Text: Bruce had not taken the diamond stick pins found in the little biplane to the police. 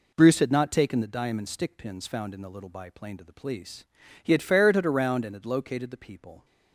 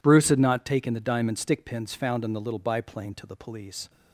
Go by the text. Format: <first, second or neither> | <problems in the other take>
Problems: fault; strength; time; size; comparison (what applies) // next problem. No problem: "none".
second | goes on to say "He had ferreted around and had located the people"; strong; from 4.2 s on; 2.2 s long